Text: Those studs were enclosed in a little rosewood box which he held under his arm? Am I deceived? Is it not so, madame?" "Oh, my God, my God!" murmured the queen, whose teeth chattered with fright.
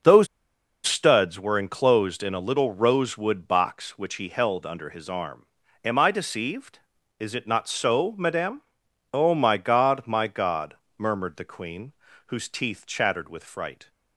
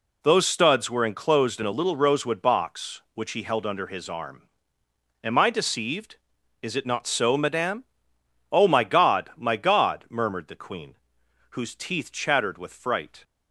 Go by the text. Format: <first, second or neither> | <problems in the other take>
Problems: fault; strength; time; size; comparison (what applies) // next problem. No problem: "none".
second | pauses between "Those" and "studs"; noticeable; at 0.2 s; 0.59 s long